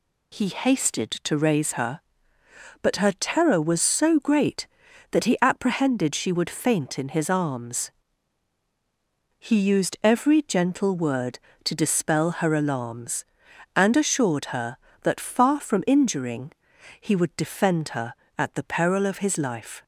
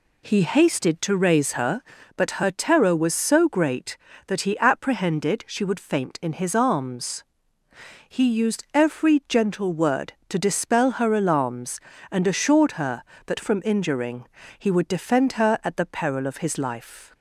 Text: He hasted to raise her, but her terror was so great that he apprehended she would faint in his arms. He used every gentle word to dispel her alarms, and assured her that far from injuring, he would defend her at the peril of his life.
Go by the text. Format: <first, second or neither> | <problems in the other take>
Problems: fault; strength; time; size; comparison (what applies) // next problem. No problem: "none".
first | skips "far"; at 13.3 s